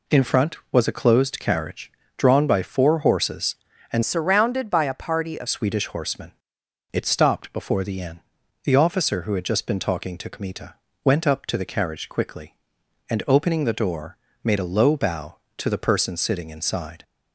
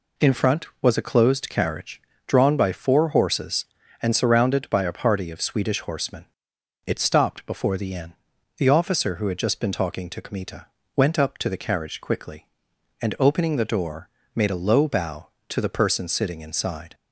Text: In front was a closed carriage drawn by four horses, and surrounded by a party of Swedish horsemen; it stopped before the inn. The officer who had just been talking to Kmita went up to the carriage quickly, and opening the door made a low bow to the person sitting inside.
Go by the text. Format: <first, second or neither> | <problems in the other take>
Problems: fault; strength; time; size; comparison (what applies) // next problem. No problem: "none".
second | pauses between "carriage" and "drawn"; slight; at 1.9 s; 0.26 s long; slight in the second // changes voice from "surrounded" to "of"; from 4.0 to 5.4 s; 1.4 s long // pauses between "Kmita" and "went"; slight; at 10.7 s; 0.28 s long; slight in the second // pauses between "door" and "made"; slight; at 14.1 s; 0.28 s long; slight in the second